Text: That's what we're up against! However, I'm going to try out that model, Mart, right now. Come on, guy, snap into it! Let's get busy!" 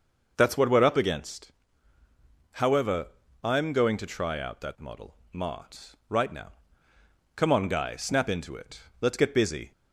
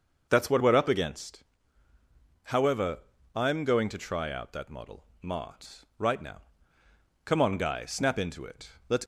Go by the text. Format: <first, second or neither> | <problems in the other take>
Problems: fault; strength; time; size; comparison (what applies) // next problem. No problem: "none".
first | starts louder than the rest; noticeable; until 1.3 s; 6 dB // stops before "get busy"; at 9.0 s